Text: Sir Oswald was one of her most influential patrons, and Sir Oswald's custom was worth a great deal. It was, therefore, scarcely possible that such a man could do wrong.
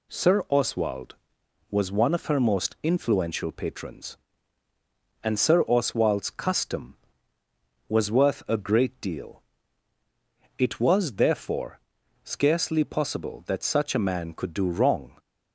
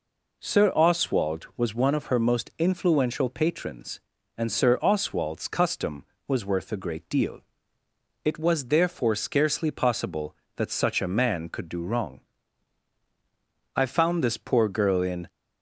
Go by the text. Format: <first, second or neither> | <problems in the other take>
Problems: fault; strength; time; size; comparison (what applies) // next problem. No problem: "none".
first | goes on to say "I found this poor girl in"; from 13.7 s on; 1.5 s long